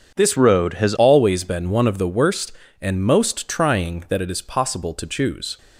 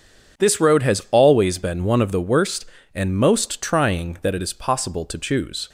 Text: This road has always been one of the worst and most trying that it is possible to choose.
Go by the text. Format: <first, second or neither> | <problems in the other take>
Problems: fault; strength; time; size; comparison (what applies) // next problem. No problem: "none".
second | starts louder than the rest; strong; until 1.1 s; 7.5 dB // changes voice from "road" to "has"; from 0.3 to 0.9 s; 0.6 s long